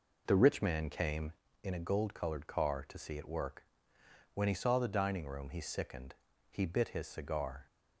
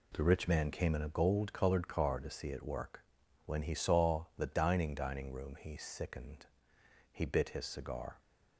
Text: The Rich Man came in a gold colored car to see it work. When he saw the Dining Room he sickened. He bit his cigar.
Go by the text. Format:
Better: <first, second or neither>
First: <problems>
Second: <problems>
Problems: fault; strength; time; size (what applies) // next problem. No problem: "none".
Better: first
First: none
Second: says "Dining" twice; at 4.9 s